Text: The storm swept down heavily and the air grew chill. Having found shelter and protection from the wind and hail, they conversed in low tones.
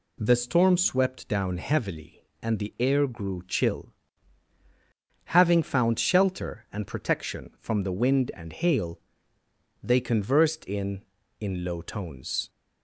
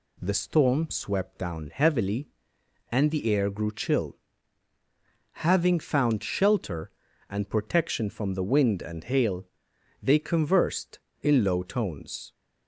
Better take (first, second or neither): second